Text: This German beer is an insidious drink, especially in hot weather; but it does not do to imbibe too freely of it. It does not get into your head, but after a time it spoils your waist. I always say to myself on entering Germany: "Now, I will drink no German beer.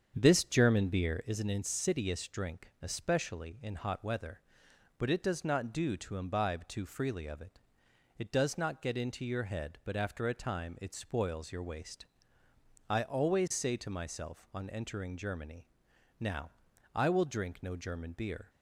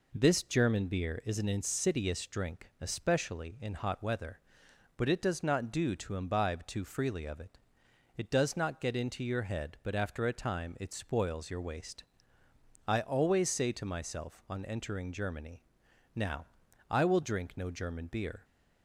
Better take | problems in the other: second | starts louder than the rest; strong; until 1.3 s; 7.5 dB

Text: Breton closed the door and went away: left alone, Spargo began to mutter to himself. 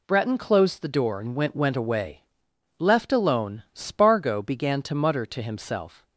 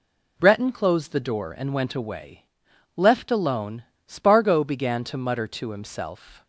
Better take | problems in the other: second | says "went" twice; at 1.5 s

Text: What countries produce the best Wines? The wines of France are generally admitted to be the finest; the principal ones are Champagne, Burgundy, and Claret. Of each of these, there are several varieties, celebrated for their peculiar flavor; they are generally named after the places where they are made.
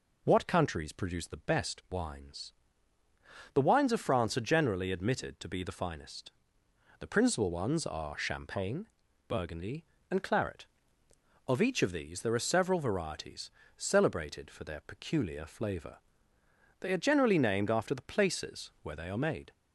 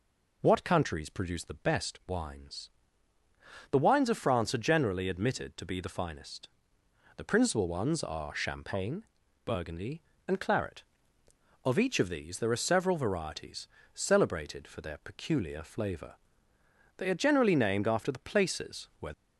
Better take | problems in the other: first | stops before "they are made"; at 19.1 s

